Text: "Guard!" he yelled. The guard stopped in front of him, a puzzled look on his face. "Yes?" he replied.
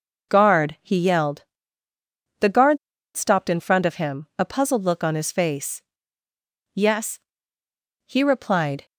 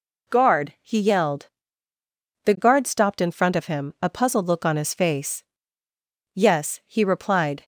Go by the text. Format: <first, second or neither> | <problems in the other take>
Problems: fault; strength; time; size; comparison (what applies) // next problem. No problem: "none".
second | pauses between "guard" and "stopped"; at 2.7 s; 0.39 s long